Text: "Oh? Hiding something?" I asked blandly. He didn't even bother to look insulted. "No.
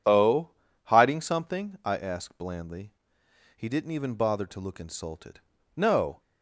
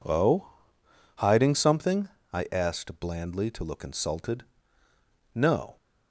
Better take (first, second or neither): first